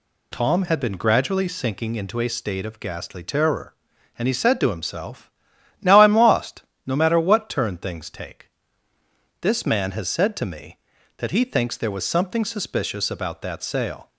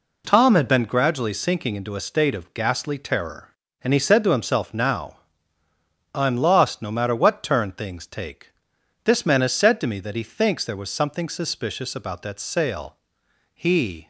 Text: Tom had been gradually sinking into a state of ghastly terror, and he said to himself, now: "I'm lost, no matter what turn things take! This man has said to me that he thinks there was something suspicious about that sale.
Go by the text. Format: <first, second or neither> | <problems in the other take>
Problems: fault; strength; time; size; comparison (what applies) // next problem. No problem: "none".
first | goes on to say "He"; from 13.5 s on; 0.54 s long